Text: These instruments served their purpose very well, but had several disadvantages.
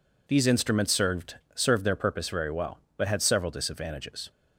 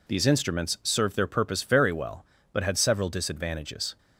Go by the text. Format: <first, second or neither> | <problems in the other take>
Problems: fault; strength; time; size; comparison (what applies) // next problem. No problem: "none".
second | says "served" twice; at 1.5 s